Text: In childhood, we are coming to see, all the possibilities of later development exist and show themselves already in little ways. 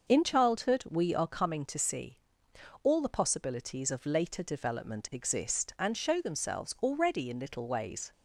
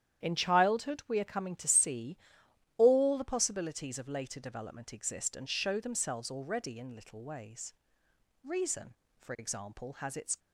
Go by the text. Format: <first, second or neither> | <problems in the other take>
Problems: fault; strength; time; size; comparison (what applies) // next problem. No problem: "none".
first | starts louder than the rest; strong; until 1.2 s; 10 dB; noticeable in the first // goes on to say "Reason for example has its"; strong; from 8.4 s on; 1.9 s long